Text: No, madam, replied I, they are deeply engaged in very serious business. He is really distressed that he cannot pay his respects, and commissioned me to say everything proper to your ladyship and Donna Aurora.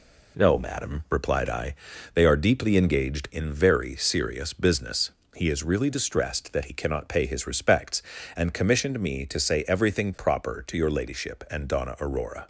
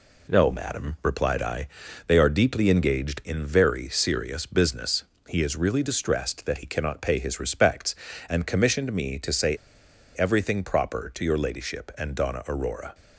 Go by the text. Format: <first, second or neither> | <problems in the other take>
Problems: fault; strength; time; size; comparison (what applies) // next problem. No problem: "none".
first | pauses between "say" and "everything"; noticeable; at 9.5 s; 0.59 s long